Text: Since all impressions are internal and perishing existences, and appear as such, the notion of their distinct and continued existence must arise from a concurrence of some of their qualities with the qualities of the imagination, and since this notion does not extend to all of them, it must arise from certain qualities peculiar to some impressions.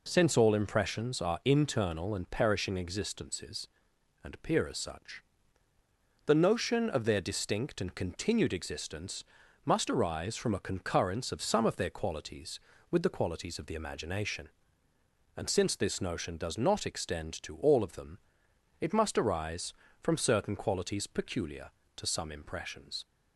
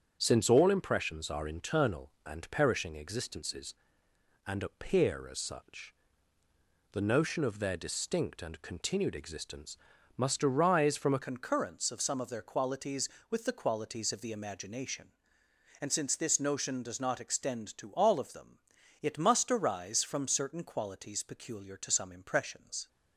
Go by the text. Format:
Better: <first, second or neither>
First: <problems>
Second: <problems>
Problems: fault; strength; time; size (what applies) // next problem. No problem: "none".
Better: first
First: pauses between "existence" and "must"; at 9.2 s; 0.40 s long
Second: starts louder than the rest; strong; until 1.2 s; 7.5 dB // pauses between "existence" and "must"; at 9.7 s; 0.40 s long // changes voice at "concurrence"; from 11.2 s on; 11.6 s long